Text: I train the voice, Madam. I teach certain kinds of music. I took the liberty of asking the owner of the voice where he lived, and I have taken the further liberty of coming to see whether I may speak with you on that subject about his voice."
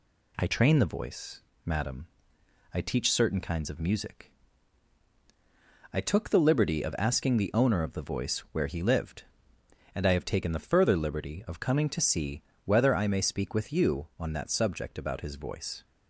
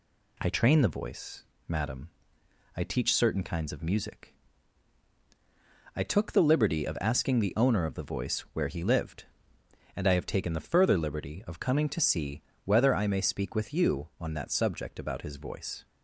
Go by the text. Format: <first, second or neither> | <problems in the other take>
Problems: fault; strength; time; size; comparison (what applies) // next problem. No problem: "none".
neither | pauses between "see" and "whether"; slight; the same in both